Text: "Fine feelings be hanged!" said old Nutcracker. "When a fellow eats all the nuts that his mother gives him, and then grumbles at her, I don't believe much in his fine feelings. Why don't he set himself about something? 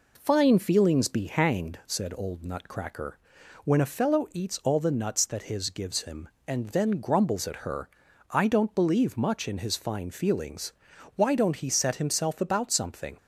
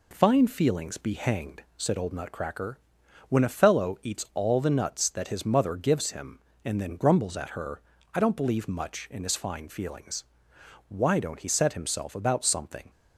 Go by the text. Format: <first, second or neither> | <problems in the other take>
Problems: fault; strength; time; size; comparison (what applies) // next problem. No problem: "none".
second | skips "mother"; at 5.6 s